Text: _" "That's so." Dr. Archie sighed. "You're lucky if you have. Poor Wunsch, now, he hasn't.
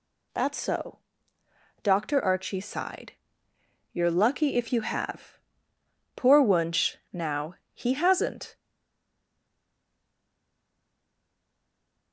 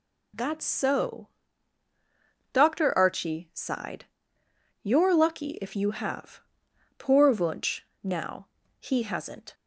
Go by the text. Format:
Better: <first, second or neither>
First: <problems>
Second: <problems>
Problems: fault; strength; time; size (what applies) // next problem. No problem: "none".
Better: second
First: stays silent after the last word; strong; from 8.5 s on; 3.6 s long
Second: none